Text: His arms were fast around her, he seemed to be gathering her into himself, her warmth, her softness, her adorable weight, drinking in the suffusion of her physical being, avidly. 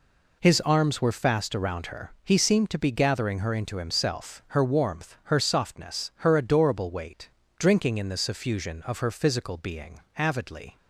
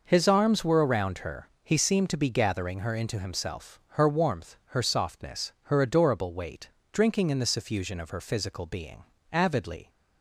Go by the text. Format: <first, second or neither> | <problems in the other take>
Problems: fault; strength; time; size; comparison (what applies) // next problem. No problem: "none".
first | skips "fast"; at 0.8 s